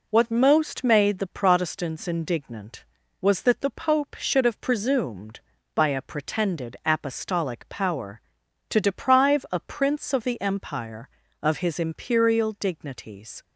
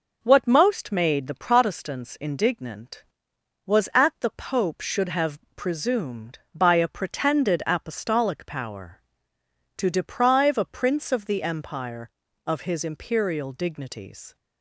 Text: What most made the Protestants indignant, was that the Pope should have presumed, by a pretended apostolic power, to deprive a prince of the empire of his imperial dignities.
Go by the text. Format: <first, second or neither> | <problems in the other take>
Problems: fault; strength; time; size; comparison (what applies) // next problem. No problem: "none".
first | says "at" for "that"; at 3.9 s // pauses between "have" and "presumed"; slight; at 5.3 s; 0.16 s long